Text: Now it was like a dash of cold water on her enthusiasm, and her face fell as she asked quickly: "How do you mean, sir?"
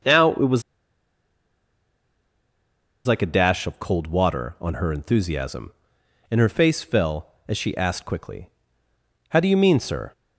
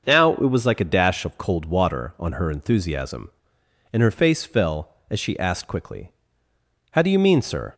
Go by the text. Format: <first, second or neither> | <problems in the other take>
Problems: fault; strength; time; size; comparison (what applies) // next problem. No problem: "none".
second | starts louder than the rest; until 3.5 s; 6.5 dB; also in the second // pauses between "was" and "like"; strong; at 0.6 s; 2.4 s long